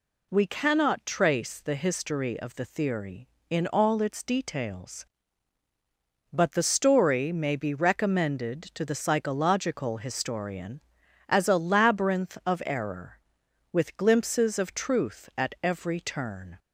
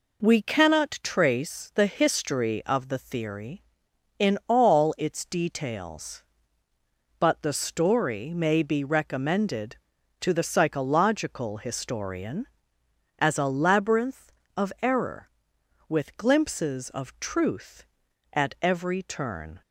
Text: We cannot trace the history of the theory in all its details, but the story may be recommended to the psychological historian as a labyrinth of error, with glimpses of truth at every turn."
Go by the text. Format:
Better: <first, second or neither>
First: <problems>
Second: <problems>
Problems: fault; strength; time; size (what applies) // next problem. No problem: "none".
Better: neither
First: none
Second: none